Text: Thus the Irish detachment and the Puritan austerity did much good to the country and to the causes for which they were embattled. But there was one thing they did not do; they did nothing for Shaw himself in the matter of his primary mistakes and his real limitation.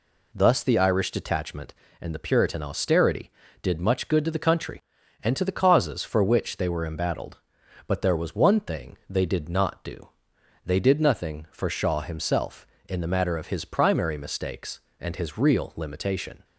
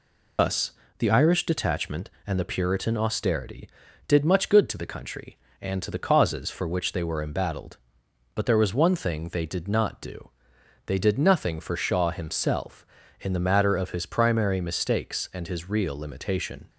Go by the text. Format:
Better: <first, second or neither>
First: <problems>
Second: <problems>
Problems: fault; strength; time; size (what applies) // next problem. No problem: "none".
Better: first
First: none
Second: loses the start of "Thus"; at 0.3 s; 105 ms // pauses between "Thus" and "the"; slight; at 0.7 s; 0.28 s long